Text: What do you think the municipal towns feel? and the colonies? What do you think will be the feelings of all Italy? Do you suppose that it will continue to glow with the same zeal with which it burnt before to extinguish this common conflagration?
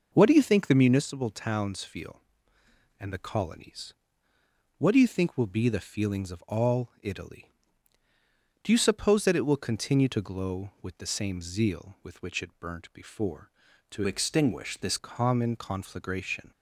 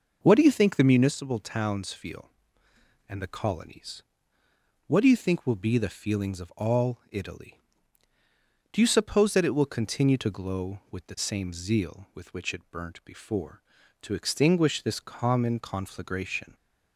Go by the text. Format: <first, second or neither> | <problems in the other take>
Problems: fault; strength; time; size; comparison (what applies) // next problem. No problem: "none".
second | changes voice from "extinguish" to "this"; from 14.0 to 14.9 s; 0.9 s long